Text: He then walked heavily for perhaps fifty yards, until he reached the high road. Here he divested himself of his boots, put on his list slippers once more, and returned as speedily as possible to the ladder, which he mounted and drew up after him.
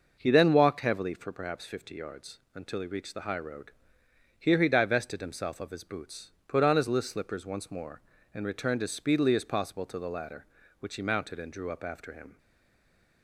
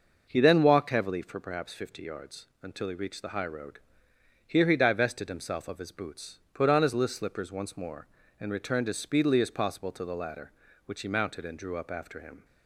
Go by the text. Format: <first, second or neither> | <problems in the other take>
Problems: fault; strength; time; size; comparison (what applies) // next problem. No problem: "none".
second | stays silent after the last word; slight; from 12.3 s on; 0.9 s long